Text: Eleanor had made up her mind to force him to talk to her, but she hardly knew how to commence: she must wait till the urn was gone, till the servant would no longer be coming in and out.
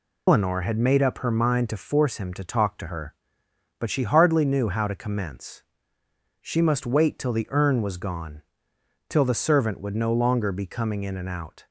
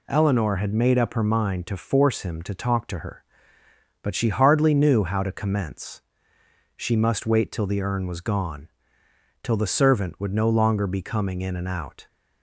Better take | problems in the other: second | loses the start of "Eleanor"; at 0.2 s; 125 ms

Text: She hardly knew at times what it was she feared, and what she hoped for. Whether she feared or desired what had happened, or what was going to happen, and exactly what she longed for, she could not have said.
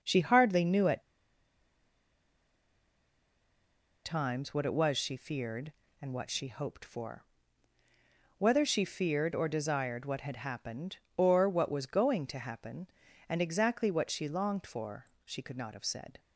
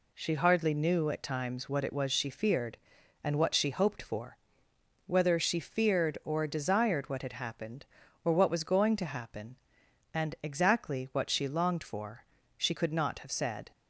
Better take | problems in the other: second | pauses between "at" and "times"; strong; at 1.0 s; 3.0 s long

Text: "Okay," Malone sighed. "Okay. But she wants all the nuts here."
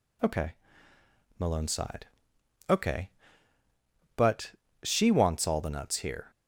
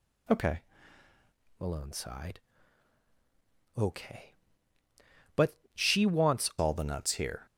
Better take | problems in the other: first | changes voice from "Malone" to "wants"; from 1.5 to 6.4 s; 4.9 s long // pauses between "But" and "she"; slight; at 5.5 s; 0.20 s long; slight in the first

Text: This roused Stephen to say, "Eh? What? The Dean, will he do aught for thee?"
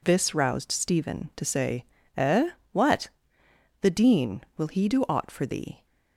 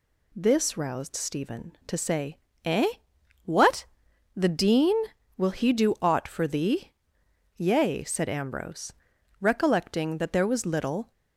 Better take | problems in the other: first | goes on to say "Yea said Ambrose recollecting that there was little"; strong; from 7.5 s on; 3.5 s long

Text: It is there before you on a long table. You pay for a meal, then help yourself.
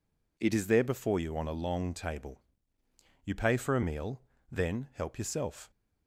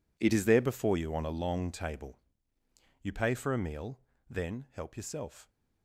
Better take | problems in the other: first | gets quieter; strong; throughout; 14.5 dB

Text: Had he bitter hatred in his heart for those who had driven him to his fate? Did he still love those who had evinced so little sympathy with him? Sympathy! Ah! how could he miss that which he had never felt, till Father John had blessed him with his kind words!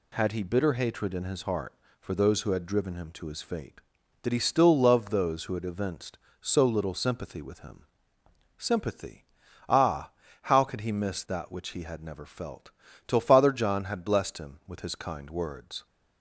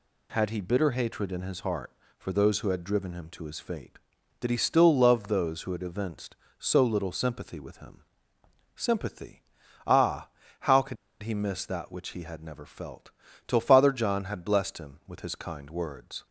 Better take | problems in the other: first | pauses between "could" and "he"; slight; at 10.9 s; 0.27 s long

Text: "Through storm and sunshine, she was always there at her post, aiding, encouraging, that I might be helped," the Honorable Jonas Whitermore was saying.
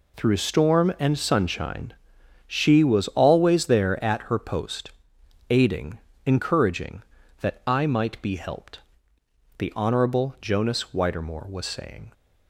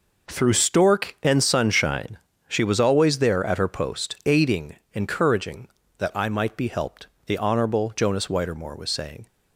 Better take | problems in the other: first | says "stork" for "storm"; at 0.5 s

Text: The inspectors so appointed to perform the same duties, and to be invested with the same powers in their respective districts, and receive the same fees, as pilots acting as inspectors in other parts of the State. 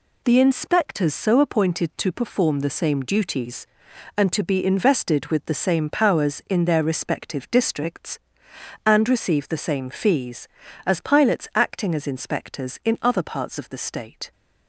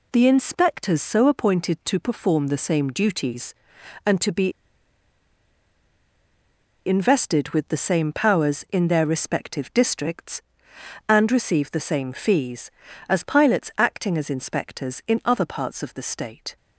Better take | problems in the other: first | pauses between "be" and "invested"; strong; at 4.5 s; 2.3 s long

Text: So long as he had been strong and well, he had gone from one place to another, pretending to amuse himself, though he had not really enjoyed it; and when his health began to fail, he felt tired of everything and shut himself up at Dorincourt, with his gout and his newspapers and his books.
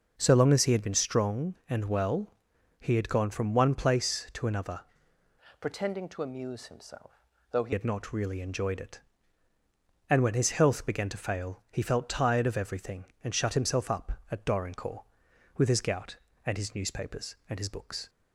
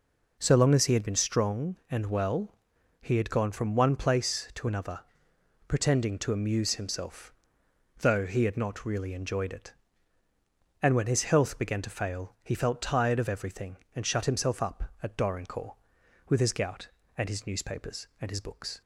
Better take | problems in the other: second | changes voice from "pretending" to "he"; from 5.5 to 7.7 s; 2.2 s long

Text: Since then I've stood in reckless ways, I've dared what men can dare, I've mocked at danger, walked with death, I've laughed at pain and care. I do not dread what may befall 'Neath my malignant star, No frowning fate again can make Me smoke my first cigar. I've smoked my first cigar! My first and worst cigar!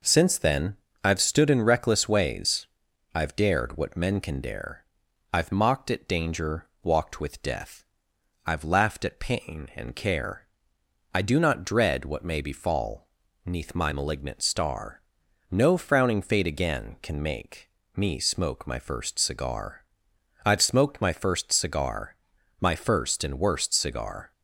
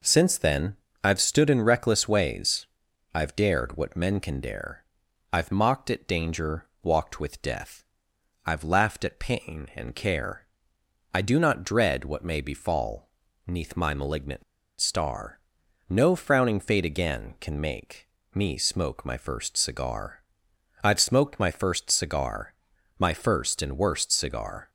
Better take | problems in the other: first | pauses between "then" and "I've"; slight; at 0.7 s; 0.30 s long; slight in the first // pauses between "befall" and "Neath"; slight; at 13.0 s; 0.36 s long; slight in the first // pauses between "malignant" and "star"; at 14.4 s; 0.36 s long // pauses between "make" and "Me"; slight; at 18.0 s; 0.24 s long; slight in the first

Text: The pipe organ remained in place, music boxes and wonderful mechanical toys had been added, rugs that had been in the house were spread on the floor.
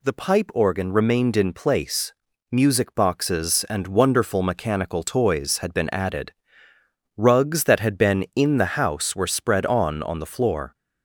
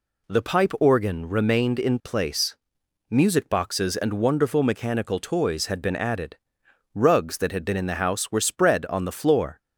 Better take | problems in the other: second | says "on" twice; at 10.0 s

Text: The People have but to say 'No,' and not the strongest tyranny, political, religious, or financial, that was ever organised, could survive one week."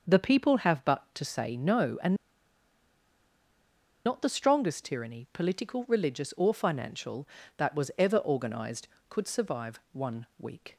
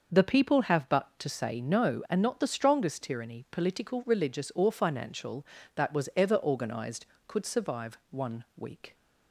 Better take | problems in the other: second | starts louder than the rest; noticeable; until 1.2 s; 6 dB; noticeable in the second // pauses between "and" and "not"; strong; at 2.1 s; 1.9 s long

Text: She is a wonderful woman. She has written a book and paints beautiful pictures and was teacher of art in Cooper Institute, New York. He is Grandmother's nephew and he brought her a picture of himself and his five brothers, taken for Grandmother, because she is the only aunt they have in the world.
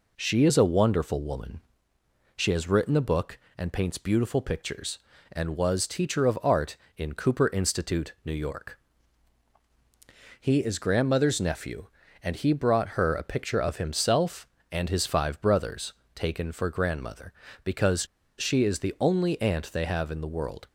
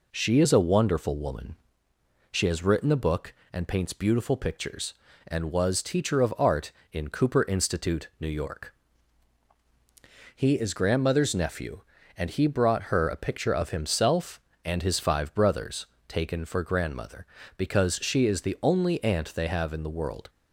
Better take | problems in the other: second | pauses between "because" and "she"; slight; at 18.0 s; 0.32 s long

